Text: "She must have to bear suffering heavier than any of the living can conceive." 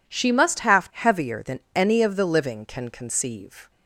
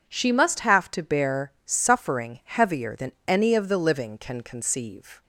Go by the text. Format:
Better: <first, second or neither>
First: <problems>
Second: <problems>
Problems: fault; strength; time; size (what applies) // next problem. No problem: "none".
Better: second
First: skips "to bear suffering"; at 0.9 s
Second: none